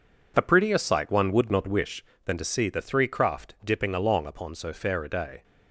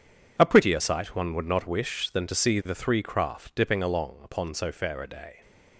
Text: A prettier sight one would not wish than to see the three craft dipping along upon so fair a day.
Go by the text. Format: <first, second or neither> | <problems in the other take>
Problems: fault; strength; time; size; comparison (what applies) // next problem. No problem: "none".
neither | none